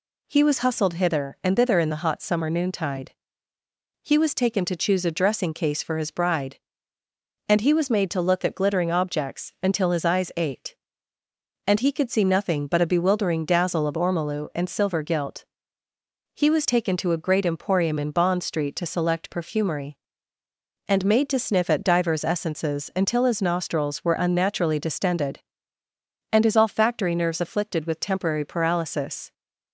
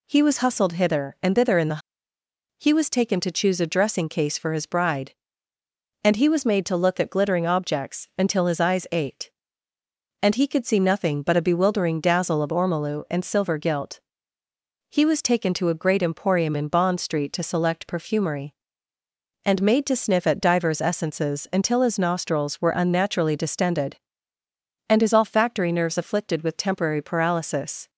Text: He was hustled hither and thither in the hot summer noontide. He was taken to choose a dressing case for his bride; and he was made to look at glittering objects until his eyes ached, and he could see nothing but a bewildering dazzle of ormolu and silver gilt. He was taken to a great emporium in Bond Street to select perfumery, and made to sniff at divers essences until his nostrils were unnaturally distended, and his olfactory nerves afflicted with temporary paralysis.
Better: first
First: none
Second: skips "hot summer noontide"; at 2.1 s

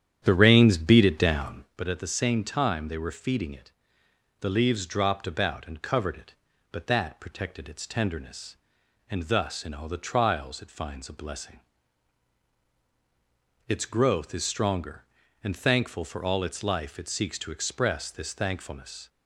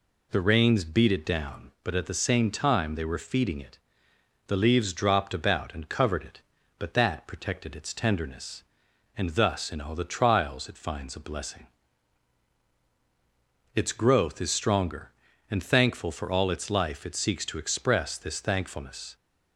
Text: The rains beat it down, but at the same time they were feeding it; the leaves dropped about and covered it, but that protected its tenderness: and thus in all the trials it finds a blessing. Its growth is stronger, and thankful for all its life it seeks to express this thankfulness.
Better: second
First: starts louder than the rest; strong; until 1.8 s; 9.5 dB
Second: none

